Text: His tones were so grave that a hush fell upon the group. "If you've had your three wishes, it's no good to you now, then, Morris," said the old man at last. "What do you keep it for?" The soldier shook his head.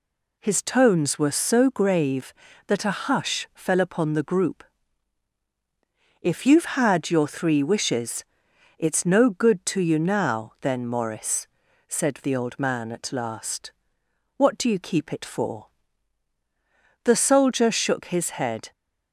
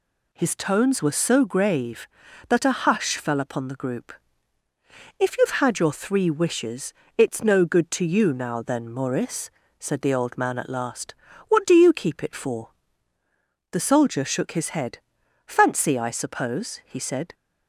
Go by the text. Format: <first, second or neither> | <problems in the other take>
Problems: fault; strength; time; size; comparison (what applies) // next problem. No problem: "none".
first | goes on to say "Fancy I suppose he said"; strong; from 15.4 s on; 1.8 s long